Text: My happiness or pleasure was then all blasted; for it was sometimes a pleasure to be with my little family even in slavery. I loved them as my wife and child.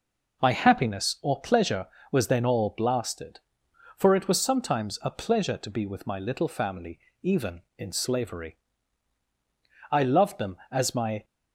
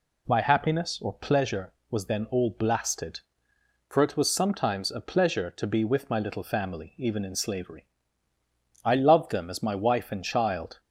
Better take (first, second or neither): second